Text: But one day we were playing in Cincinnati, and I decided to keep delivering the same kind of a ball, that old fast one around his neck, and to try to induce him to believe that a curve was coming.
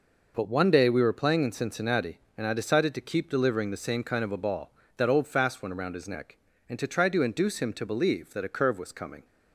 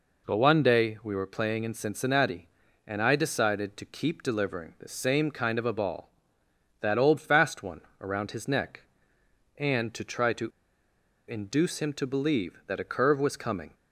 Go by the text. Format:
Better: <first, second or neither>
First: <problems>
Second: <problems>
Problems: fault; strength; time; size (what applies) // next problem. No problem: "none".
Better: first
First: none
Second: pauses between "one" and "around"; slight; at 7.8 s; 0.20 s long // pauses between "to" and "induce"; noticeable; at 10.4 s; 0.78 s long